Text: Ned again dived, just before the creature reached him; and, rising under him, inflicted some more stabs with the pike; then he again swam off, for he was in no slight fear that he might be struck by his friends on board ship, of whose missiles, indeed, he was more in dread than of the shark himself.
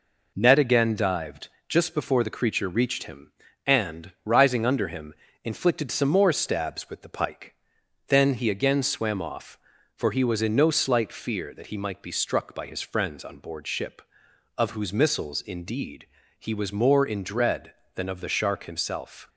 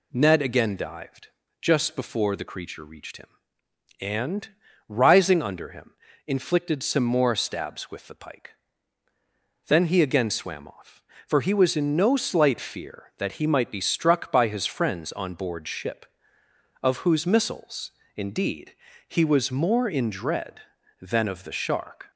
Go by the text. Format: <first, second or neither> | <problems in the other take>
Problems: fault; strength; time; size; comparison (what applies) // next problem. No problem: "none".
first | stops before "himself"; at 22.1 s